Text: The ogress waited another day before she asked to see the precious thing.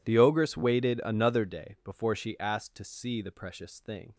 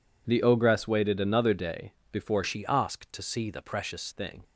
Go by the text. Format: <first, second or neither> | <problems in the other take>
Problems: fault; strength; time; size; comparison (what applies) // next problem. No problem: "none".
first | pauses between "day" and "before"; slight; at 1.9 s; 0.16 s long // changes voice from "she" to "precious"; from 2.4 to 4.1 s; 1.7 s long